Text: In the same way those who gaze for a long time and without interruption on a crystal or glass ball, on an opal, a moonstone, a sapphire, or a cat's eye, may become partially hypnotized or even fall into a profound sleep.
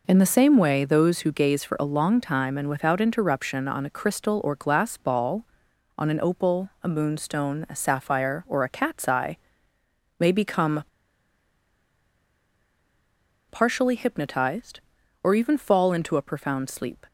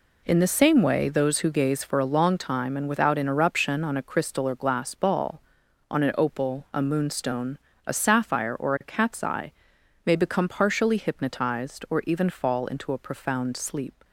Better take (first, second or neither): second